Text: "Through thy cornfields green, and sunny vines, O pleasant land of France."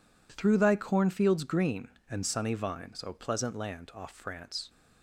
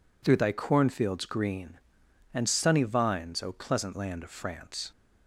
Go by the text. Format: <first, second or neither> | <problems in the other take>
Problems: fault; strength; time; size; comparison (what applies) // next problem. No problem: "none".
second | says "off" for "of"; at 3.9 s